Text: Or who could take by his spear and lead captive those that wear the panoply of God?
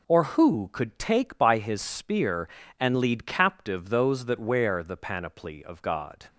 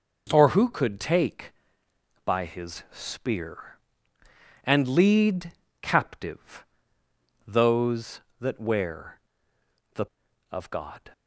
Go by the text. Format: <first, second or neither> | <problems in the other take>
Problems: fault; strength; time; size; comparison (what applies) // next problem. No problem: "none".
first | pauses between "lead" and "captive"; slight; at 5.5 s; 0.28 s long // pauses between "captive" and "those"; noticeable; at 6.6 s; 0.82 s long // pauses between "wear" and "the"; noticeable; at 9.1 s; 0.74 s long // skips "panoply"; at 10.2 s